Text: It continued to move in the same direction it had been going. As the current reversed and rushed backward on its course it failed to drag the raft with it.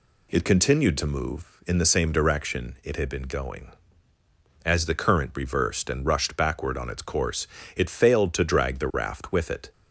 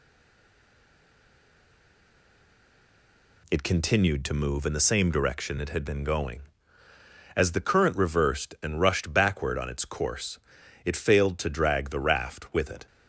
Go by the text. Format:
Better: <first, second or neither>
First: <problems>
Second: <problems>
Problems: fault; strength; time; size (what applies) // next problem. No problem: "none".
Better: first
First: pauses between "course" and "it"; slight; at 7.4 s; 0.28 s long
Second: stays silent before the first word; strong; until 3.4 s; 3.4 s long // pauses between "course" and "it"; noticeable; at 10.3 s; 0.46 s long